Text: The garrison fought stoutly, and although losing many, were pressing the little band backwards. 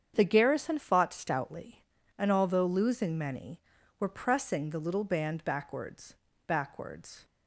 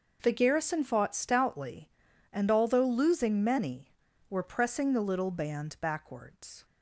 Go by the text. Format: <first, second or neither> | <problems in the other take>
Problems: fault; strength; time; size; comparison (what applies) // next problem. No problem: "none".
second | starts louder than the rest; strong; until 1.1 s; 8 dB; noticeable in the second // says "backwards" twice; at 6.4 s